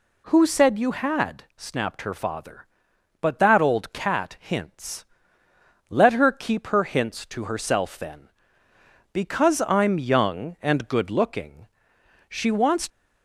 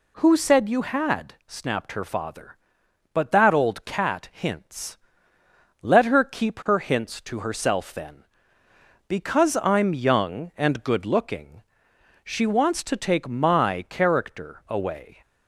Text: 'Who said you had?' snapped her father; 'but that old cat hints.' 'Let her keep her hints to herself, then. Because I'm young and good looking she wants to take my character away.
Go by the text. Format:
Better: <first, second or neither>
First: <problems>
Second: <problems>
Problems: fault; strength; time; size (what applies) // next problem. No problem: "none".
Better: second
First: pauses between "looking" and "she"; noticeable; at 11.6 s; 0.66 s long // stops before "to take my character away"; at 12.8 s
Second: pauses between "looking" and "she"; noticeable; at 11.6 s; 0.66 s long